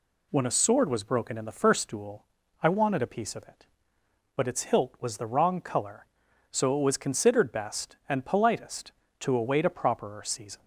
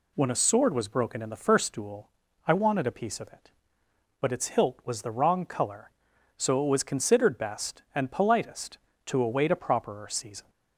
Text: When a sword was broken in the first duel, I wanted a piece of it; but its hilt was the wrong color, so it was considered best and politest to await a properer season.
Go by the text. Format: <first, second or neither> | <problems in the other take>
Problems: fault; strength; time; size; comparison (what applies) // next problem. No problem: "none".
neither | none